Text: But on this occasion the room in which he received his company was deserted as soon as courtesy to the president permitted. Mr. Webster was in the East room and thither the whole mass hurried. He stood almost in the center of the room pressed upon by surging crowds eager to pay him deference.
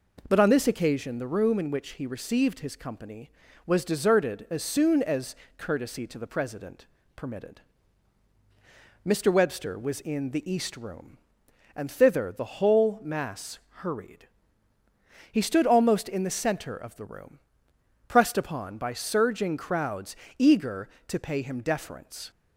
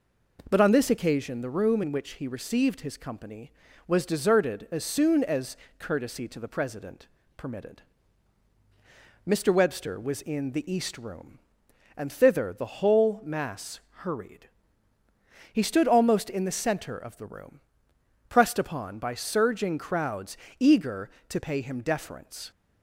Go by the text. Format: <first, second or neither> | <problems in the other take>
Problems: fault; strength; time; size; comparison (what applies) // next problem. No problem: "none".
neither | pauses between "as" and "courtesy"; slight; the same in both // pauses between "president" and "permitted"; slight; the same in both // pauses between "mass" and "hurried"; slight; the same in both // pauses between "room" and "pressed"; noticeable; the same in both // pauses between "crowds" and "eager"; slight; the same in both